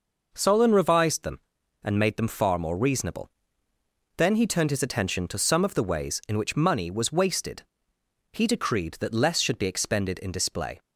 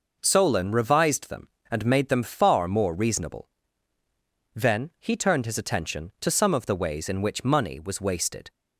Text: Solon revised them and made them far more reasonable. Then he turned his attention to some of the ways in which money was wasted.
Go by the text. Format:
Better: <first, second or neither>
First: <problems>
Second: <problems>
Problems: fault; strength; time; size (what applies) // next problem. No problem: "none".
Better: second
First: goes on to say "He decreed that less should be expended in display"; strong; from 8.3 s on; 2.4 s long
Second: none